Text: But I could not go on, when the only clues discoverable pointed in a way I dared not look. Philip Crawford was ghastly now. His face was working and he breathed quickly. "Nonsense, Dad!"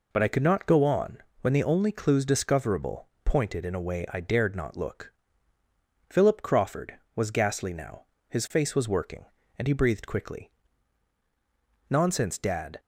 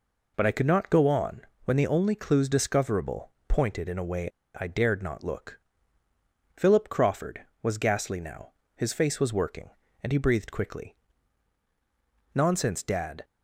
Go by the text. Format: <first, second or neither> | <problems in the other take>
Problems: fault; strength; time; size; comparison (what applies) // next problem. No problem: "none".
first | pauses between "discoverable" and "pointed"; slight; at 3.3 s; 0.18 s long; slight in the first // pauses between "way" and "I"; slight; at 4.2 s; 0.31 s long